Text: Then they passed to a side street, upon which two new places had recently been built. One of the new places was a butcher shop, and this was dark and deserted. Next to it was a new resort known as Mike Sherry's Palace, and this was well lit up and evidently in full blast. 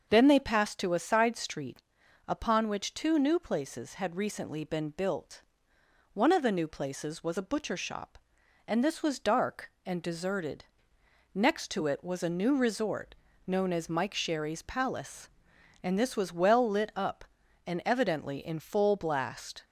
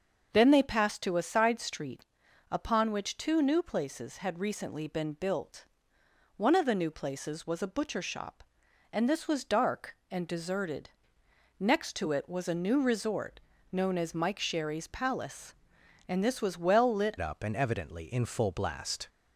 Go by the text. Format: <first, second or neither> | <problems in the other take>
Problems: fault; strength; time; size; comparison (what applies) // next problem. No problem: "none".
first | starts louder than the rest; until 1.3 s; 6 dB; also in the first // pauses between "resort" and "known"; slight; at 13.4 s; 0.32 s long; slight in the first // changes voice at "up"; from 17.1 s on; 1.9 s long